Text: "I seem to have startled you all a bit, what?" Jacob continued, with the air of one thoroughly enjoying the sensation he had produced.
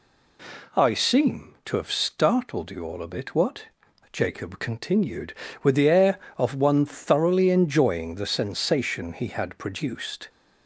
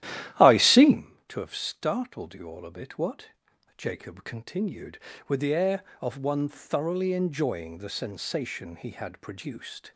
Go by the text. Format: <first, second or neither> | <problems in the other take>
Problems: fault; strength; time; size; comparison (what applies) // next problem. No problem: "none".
first | starts louder than the rest; strong; until 1.0 s; 12.5 dB